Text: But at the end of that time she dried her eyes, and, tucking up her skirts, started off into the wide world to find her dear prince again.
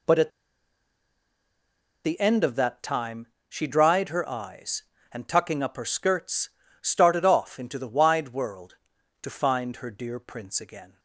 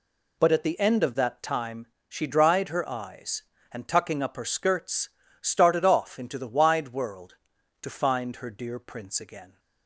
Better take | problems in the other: second | pauses between "at" and "the"; strong; at 0.2 s; 1.7 s long // pauses between "time" and "she"; slight; at 3.2 s; 0.20 s long; slight in the second

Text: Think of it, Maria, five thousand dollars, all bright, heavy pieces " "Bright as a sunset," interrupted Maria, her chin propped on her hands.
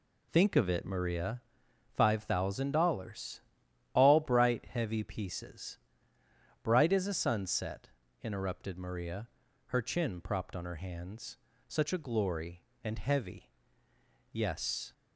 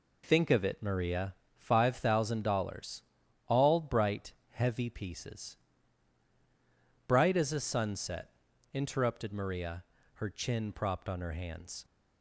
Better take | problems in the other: second | goes on to say "Such a glory and heavy Yes"; strong; from 11.6 s on; 3.2 s long

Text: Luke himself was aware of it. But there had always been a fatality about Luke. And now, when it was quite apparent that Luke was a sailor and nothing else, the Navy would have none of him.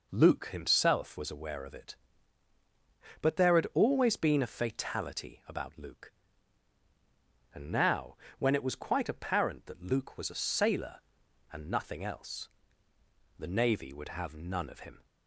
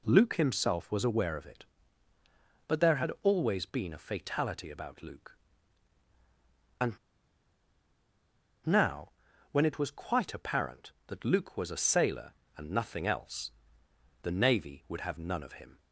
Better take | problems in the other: first | pauses between "And" and "now"; strong; at 6.9 s; 1.7 s long

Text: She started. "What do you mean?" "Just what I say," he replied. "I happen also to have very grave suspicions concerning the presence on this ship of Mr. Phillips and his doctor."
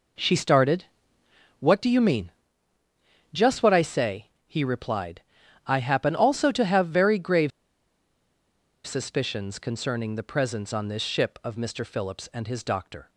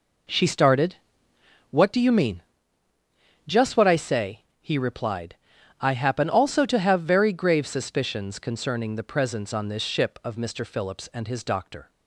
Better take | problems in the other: second | pauses between "grave" and "suspicions"; strong; at 7.5 s; 1.3 s long

